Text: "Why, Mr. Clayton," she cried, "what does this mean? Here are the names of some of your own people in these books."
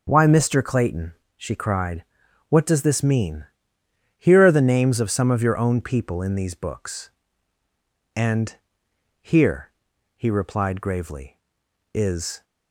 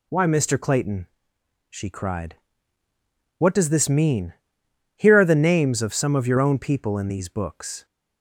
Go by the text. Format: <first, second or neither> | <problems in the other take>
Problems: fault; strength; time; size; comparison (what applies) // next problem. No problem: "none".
second | starts louder than the rest; until 1.0 s; 6.5 dB // goes on to say "And here he replied gravely is"; strong; from 8.1 s on; 4.2 s long